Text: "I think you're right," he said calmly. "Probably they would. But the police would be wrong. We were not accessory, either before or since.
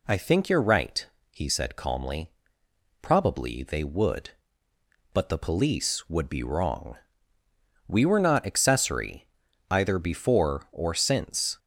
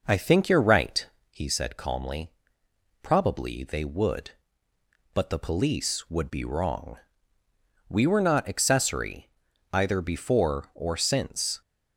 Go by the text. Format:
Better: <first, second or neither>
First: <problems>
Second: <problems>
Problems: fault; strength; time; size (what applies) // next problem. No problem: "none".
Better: first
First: none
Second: starts louder than the rest; noticeable; until 1.3 s; 5 dB